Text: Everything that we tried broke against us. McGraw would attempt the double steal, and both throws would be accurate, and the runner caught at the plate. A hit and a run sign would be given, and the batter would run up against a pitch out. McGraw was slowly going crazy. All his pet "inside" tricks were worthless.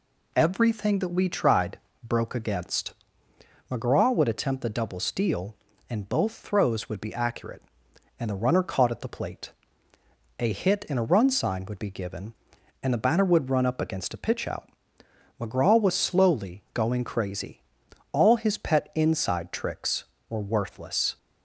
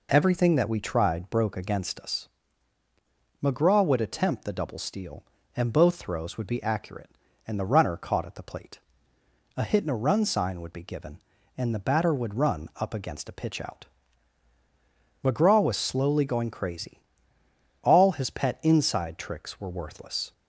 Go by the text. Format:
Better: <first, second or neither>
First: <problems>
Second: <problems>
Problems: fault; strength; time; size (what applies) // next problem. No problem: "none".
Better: second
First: pauses between "tried" and "broke"; slight; at 1.7 s; 0.30 s long // skips "us"; at 3.3 s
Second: none